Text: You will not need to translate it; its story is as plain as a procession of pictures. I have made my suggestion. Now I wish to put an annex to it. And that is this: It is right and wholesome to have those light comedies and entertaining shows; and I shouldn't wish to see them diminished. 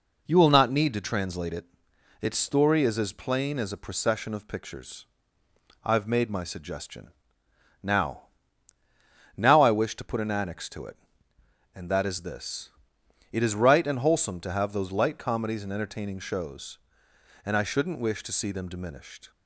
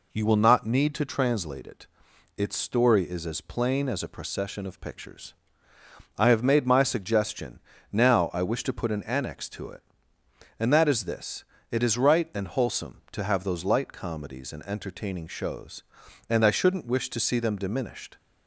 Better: second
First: says "Now" twice; at 9.3 s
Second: none

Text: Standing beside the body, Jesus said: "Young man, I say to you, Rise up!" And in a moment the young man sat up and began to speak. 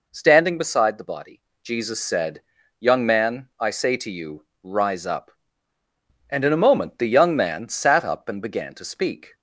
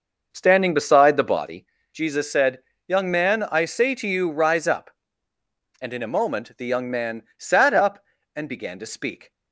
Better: first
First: none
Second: starts louder than the rest; noticeable; until 1.6 s; 6 dB

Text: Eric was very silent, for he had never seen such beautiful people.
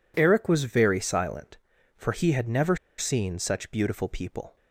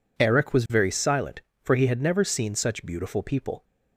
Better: second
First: pauses between "never" and "seen"; slight; at 2.7 s; 0.23 s long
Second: none

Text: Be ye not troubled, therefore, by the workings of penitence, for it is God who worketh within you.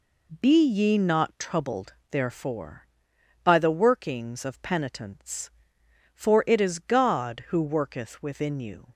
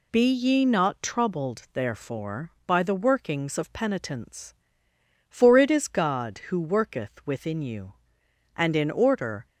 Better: first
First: none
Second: goes on to say "And in order"; noticeable; from 8.5 s on; 0.90 s long

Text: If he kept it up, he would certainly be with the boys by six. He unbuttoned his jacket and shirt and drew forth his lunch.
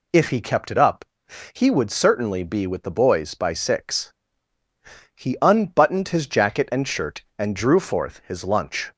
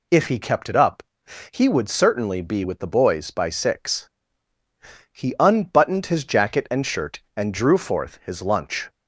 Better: neither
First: none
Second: none

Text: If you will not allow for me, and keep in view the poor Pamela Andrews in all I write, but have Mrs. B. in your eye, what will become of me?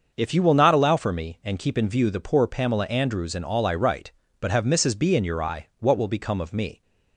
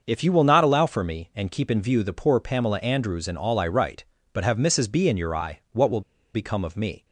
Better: first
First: starts louder than the rest; until 1.1 s; 6.5 dB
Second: starts louder than the rest; until 1.0 s; 6.5 dB // pauses between "will" and "become"; slight; at 6.0 s; 0.33 s long

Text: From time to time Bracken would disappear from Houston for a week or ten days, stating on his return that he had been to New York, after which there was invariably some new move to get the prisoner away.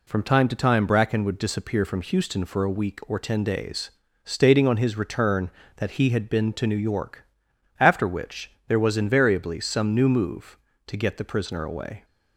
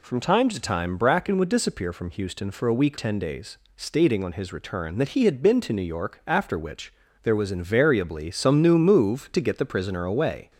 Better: first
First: pauses between "which" and "there"; slight; at 8.5 s; 0.16 s long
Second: skips "or"; at 2.9 s // pauses between "which" and "there"; slight; at 6.9 s; 0.30 s long

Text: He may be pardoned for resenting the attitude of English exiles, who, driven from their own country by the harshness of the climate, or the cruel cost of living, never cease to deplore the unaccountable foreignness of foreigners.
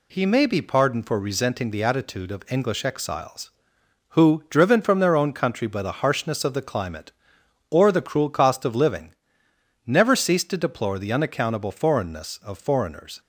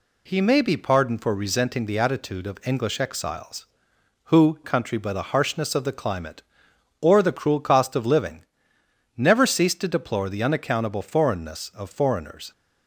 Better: first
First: none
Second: skips "driven from their own"; at 4.6 s

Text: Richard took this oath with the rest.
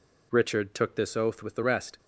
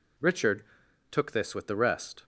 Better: first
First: none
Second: pauses between "Richard" and "took"; noticeable; at 0.6 s; 0.48 s long // skips "oath"; at 1.5 s

